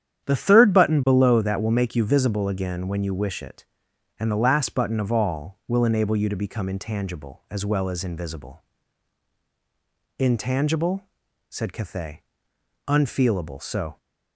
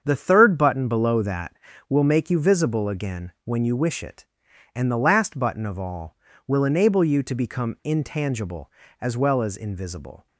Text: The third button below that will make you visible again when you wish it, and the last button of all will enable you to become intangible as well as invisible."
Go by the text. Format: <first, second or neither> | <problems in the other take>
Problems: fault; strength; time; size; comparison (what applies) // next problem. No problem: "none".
second | starts louder than the rest; strong; until 1.3 s; 10 dB; strong in the second // goes on to say "Intangible said Cathay Unfeelable so"; strong; from 10.1 s on; 3.8 s long